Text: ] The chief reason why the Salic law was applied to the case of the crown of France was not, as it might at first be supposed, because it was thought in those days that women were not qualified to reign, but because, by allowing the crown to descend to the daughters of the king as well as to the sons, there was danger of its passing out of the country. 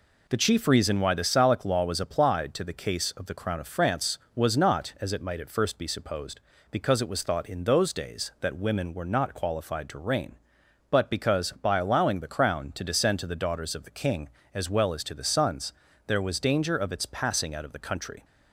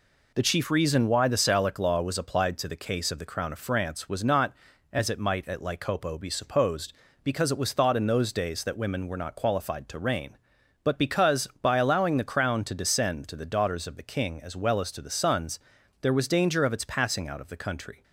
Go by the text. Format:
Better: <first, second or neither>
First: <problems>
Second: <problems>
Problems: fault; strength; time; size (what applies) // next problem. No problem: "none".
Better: first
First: none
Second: says "lycopo" for "first"; at 5.5 s